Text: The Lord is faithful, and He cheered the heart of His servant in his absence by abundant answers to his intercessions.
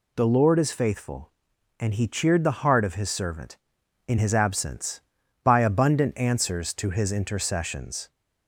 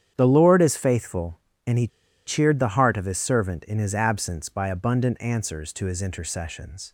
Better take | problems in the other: first | starts louder than the rest; strong; until 1.1 s; 9 dB // pauses between "He" and "cheered"; at 1.8 s; 0.38 s long

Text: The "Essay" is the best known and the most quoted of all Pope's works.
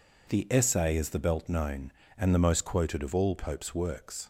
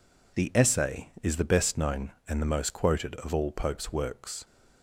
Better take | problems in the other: second | says "belt" for "best"; at 1.1 s

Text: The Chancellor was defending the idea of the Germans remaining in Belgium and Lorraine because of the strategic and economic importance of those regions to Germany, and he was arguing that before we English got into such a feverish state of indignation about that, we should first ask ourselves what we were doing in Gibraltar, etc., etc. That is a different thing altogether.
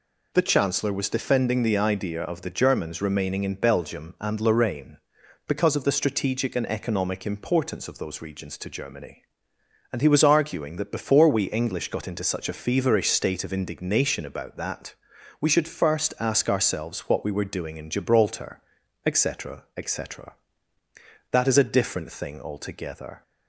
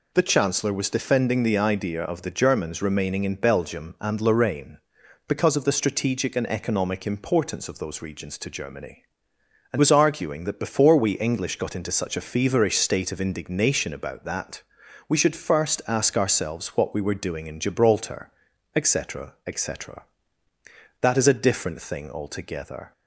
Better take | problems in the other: first | skips "he"; at 9.7 s

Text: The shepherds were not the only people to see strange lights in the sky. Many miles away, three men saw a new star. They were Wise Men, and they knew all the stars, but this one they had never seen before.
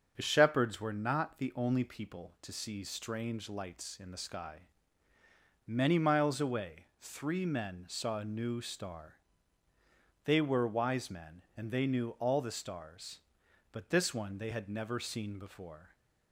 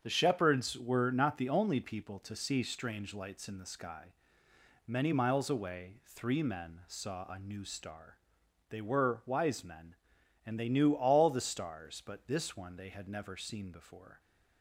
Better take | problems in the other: neither | starts louder than the rest; the same in both

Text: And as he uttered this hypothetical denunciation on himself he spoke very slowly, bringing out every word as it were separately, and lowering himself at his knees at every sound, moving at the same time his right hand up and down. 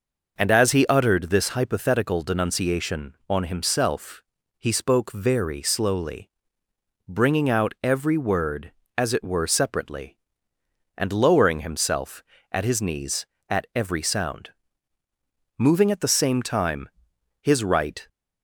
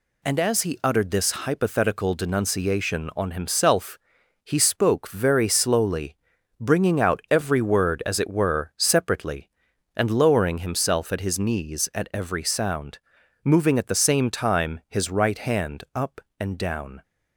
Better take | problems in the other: second | pauses between "himself" and "he"; slight; at 4.2 s; 0.36 s long; noticeable in the second // pauses between "time" and "his"; noticeable; at 16.8 s; 0.54 s long // stops before "hand up and down"; at 18.0 s

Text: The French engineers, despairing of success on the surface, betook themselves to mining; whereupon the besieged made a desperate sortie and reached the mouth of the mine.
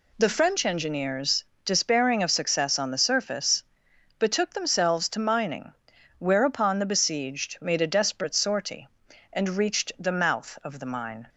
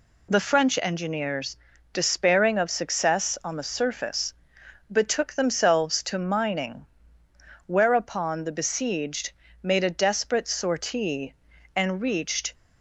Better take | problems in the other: first | pauses between "besieged" and "made"; slight; at 9.3 s; 0.32 s long // stops before "the mouth of the mine"; at 12.5 s

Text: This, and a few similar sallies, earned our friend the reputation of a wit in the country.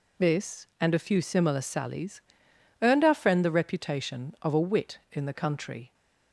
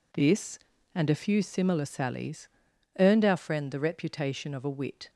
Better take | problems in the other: first | stops before "in the country"; at 5.0 s

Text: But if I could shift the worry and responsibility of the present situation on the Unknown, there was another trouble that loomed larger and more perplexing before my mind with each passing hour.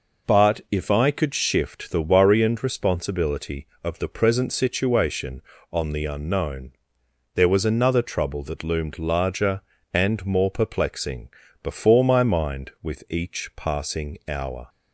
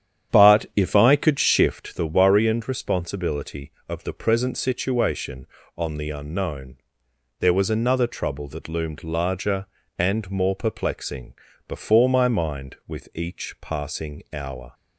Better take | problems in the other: first | starts louder than the rest; strong; until 1.9 s; 9.5 dB // pauses between "perplexing" and "before"; slight; at 11.3 s; 0.34 s long; slight in the first

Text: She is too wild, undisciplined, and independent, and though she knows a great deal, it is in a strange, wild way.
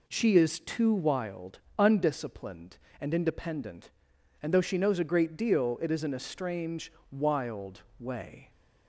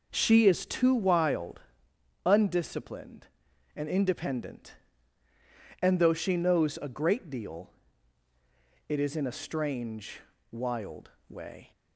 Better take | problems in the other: neither | pauses between "wild" and "way"; slight; the same in both

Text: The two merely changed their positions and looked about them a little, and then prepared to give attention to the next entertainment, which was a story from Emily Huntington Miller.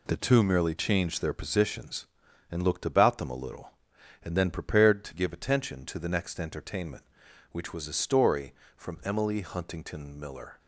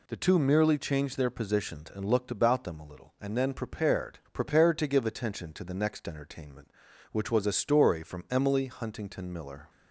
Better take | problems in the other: first | says "prepared" twice; at 4.3 s

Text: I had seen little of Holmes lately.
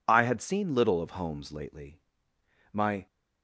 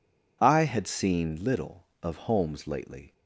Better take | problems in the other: second | goes on to say "My"; slight; from 2.7 s on; 0.34 s long

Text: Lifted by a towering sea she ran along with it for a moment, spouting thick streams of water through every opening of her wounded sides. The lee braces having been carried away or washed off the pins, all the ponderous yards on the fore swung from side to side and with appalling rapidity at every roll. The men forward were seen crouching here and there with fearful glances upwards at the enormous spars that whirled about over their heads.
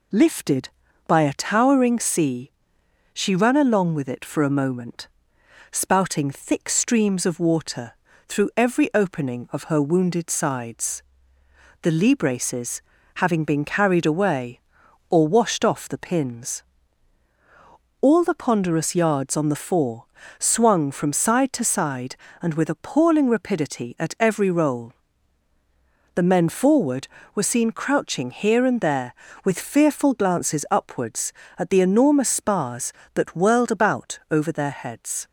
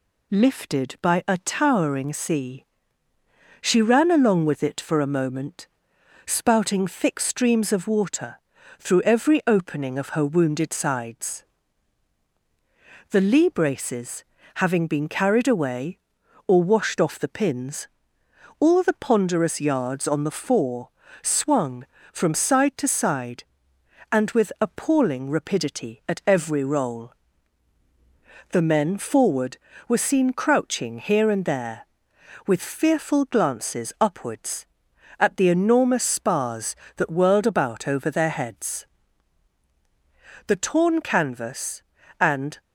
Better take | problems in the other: first | pauses between "sea" and "she"; noticeable; at 2.6 s; 0.98 s long; noticeable in the first // pauses between "water" and "through"; at 8.3 s; 0.40 s long; also in the first // pauses between "braces" and "having"; slight; at 14.2 s; 0.32 s long; slight in the first // pauses between "fore" and "swung"; slight; at 20.8 s; 0.34 s long; slight in the first // goes on to say "The torn canvas and"; strong; from 40.4 s on; 2.1 s long

